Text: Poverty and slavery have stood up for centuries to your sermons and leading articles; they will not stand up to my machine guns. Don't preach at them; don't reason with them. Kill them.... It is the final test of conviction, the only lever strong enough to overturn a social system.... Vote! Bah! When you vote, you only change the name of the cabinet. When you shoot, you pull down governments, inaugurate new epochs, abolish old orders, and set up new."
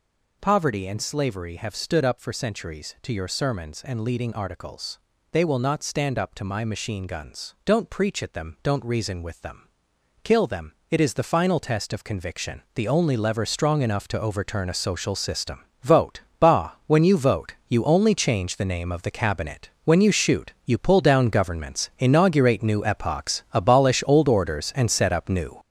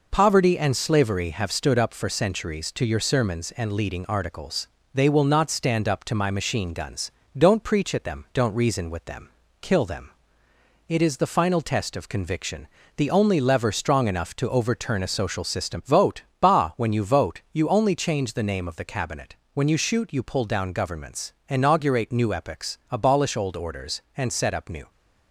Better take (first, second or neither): second